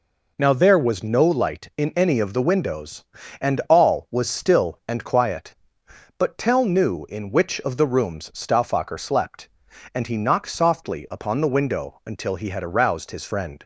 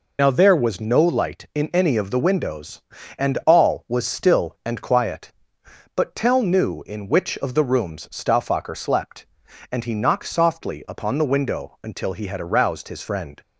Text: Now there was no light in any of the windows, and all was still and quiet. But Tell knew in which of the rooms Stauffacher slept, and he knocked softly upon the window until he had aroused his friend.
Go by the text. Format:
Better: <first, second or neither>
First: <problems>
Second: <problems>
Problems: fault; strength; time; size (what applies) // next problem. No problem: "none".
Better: first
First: none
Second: loses the start of "Now"; at 0.1 s; 60 ms